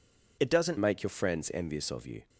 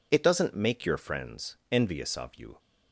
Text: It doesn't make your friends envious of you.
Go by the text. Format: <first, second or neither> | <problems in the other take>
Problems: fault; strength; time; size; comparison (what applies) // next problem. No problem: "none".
second | changes voice at "make"; from 0.7 s on; 1.5 s long